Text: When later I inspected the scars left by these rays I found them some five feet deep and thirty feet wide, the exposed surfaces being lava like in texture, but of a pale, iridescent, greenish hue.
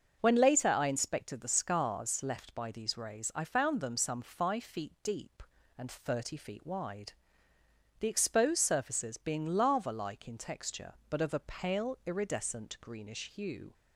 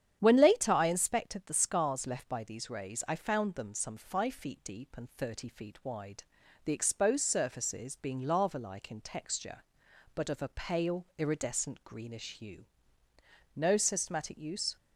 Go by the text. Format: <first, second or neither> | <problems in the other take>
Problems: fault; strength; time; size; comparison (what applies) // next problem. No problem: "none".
first | starts louder than the rest; strong; until 1.2 s; 9 dB; also in the first // goes on to say "No systematic use"; noticeable; from 13.5 s on; 1.2 s long